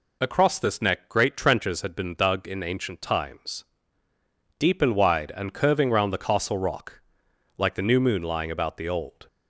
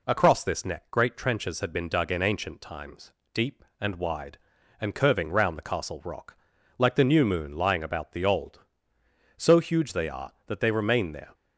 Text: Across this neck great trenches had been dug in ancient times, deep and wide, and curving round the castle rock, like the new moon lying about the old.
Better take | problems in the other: first | goes on to say "So huge they are that they remain there"; strong; from 9.3 s on; 1.9 s long

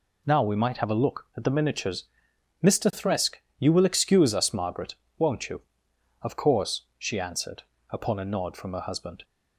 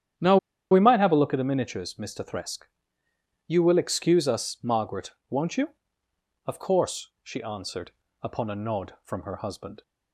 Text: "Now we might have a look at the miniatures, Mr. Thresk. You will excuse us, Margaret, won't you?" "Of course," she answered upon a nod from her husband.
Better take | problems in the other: first | starts louder than the rest; strong; until 1.5 s; 10 dB // pauses between "Now" and "we"; slight; at 0.3 s; 0.33 s long // pauses between "answered" and "upon"; slight; at 7.9 s; 0.32 s long; slight in the first

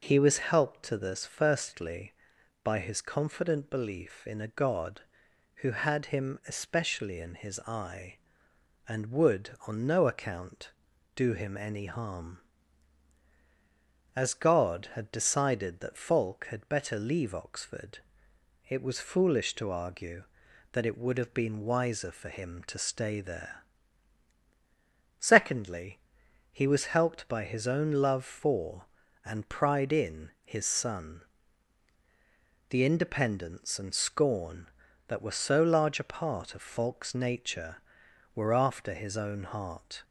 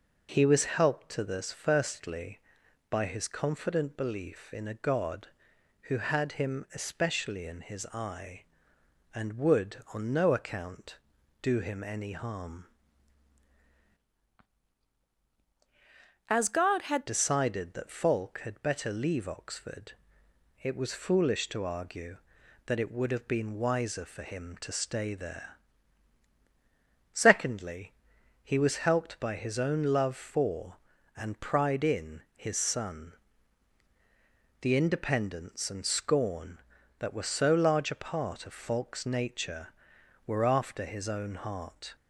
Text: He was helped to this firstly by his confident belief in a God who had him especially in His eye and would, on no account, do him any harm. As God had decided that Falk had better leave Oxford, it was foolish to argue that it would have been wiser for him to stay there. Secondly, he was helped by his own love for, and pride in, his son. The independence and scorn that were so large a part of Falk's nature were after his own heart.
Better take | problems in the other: first | changes voice from "As" to "had"; from 16.2 to 17.0 s; 0.8 s long

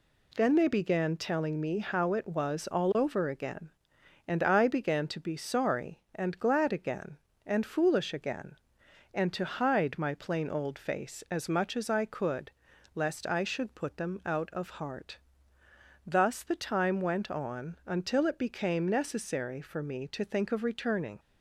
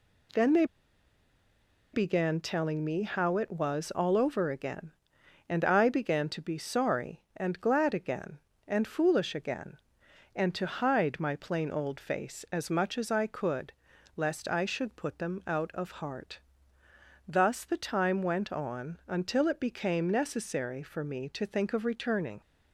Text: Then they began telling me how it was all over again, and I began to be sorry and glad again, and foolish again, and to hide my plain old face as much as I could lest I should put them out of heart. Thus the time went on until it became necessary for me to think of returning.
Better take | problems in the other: first | pauses between "they" and "began"; strong; at 0.6 s; 1.2 s long // pauses between "could" and "lest"; noticeable; at 13.7 s; 0.46 s long; noticeable in the first

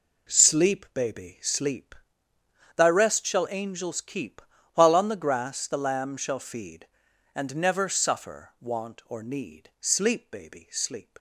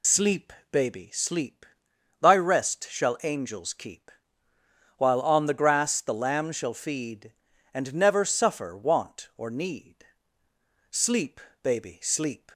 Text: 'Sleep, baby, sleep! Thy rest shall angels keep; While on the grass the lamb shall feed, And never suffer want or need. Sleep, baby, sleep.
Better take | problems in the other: first | loses the start of "Sleep"; at 0.0 s; 45 ms

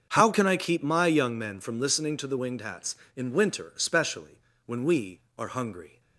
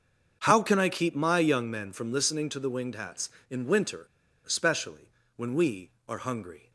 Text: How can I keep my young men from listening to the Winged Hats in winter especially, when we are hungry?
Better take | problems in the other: first | starts louder than the rest; until 1.4 s; 6.5 dB; also in the first // pauses between "winter" and "especially"; at 4.0 s; 0.40 s long

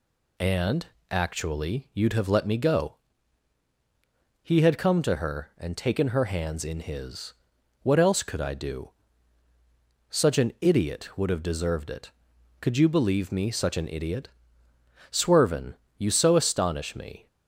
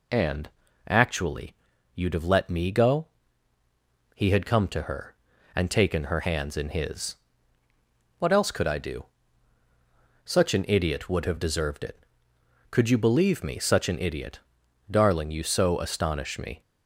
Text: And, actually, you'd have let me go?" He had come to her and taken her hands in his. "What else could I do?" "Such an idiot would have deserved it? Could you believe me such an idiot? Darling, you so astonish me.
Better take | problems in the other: second | says "Swervin" for "Darling"; at 15.1 s

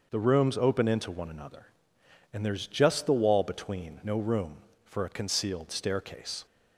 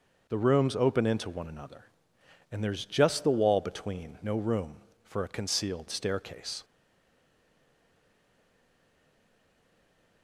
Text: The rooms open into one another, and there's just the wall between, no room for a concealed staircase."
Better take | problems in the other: first | stays silent after the last word; strong; from 6.6 s on; 3.6 s long

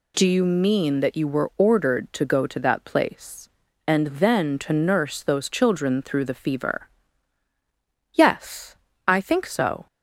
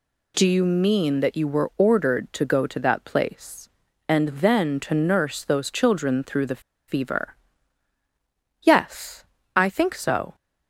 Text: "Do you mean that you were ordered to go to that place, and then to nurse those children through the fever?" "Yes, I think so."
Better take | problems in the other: first | pauses between "the" and "fever"; slight; at 6.5 s; 0.28 s long

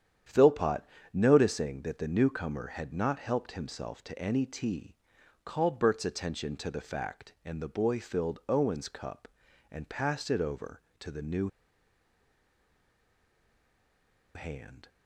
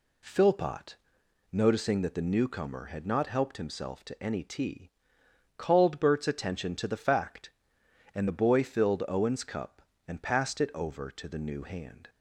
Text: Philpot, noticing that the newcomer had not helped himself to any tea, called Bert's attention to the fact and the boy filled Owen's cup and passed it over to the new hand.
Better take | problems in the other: second | starts louder than the rest; strong; until 1.5 s; 9 dB // pauses between "new" and "hand"; strong; at 11.4 s; 2.8 s long

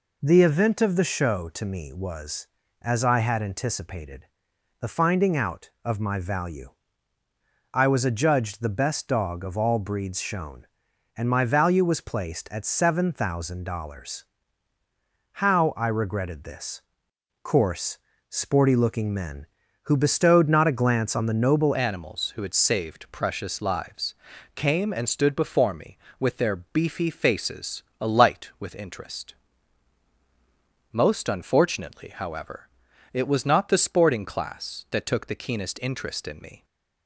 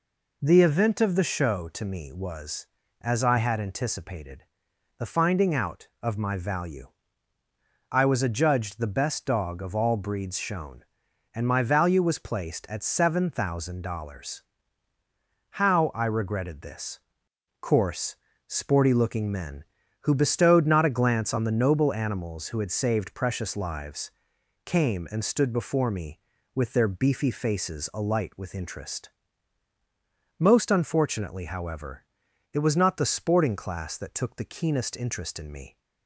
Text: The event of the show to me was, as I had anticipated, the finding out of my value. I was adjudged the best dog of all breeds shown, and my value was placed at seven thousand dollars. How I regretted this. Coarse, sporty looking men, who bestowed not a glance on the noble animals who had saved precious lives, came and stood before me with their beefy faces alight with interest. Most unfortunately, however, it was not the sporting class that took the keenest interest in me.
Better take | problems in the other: second | changes voice at "animals"; from 21.7 s on; 14.9 s long // pauses between "faces" and "alight"; slight; at 27.8 s; 0.16 s long

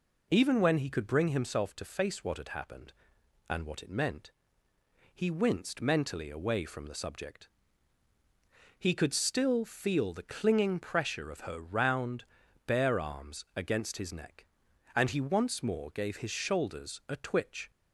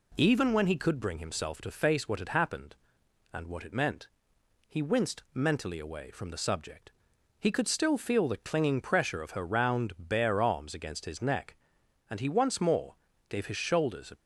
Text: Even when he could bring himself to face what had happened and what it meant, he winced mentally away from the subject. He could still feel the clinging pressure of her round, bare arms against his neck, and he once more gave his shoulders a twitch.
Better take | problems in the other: first | pauses between "more" and "gave"; slight; at 12.9 s; 0.34 s long // stops before "twitch"; at 14.1 s

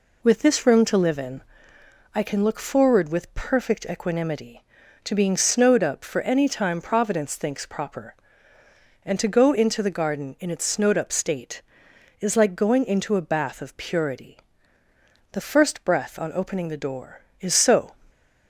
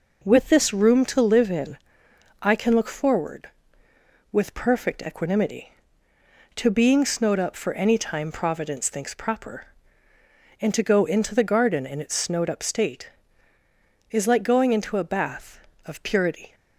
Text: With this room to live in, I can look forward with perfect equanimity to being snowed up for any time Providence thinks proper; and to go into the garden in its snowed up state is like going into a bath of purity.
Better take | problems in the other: second | goes on to say "The first breath on opening the door is so"; strong; from 15.3 s on; 2.6 s long

